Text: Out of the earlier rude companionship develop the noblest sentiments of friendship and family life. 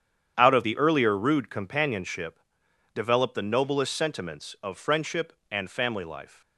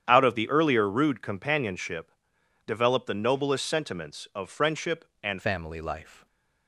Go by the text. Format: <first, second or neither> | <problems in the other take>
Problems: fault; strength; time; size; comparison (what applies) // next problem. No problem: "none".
first | starts louder than the rest; strong; until 1.1 s; 9 dB; strong in the first // pauses between "companionship" and "develop"; noticeable; at 2.1 s; 0.56 s long; noticeable in the first // changes voice at "family"; from 5.4 s on; 0.8 s long